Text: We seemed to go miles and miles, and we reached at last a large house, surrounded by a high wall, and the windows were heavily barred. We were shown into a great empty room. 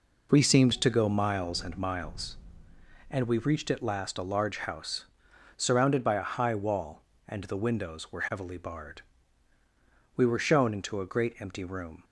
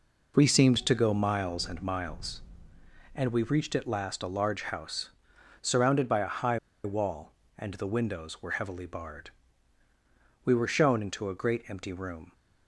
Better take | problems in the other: first | pauses between "high" and "wall"; slight; at 6.5 s; 0.25 s long

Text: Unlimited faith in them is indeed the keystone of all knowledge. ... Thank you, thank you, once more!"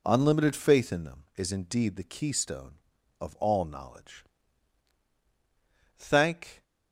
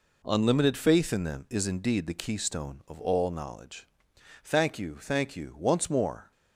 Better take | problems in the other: second | stops before "you thank you once more"; at 6.6 s

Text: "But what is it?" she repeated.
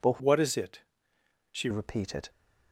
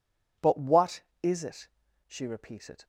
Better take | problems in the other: second | changes voice from "what" to "she"; from 0.1 to 1.6 s; 1.5 s long

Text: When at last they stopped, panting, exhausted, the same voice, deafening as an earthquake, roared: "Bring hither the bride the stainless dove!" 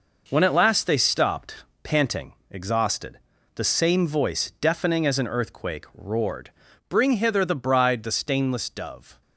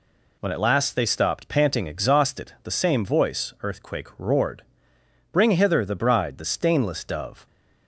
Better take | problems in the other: first | skips "deafening as an"; at 3.5 s

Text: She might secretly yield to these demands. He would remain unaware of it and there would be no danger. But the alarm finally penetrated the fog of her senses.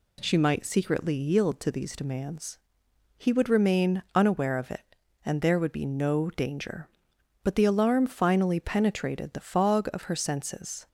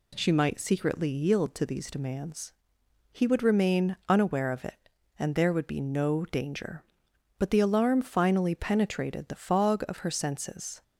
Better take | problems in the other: neither | none

